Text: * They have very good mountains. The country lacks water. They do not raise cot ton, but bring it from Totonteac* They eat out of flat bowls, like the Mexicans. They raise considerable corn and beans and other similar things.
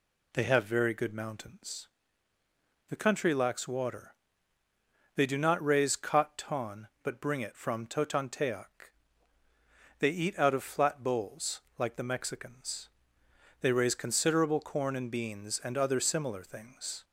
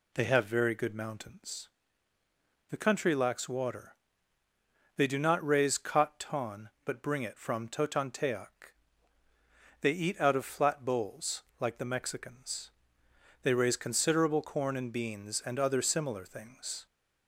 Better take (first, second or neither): neither